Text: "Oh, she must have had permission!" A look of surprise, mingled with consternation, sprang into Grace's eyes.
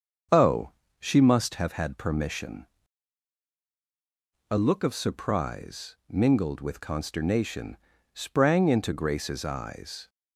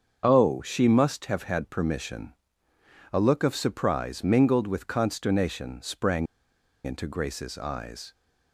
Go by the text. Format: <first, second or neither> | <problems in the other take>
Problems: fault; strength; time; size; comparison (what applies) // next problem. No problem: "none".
first | starts louder than the rest; until 1.2 s; 6.5 dB; strong in the first // pauses between "sprang" and "into"; noticeable; at 6.2 s; 0.58 s long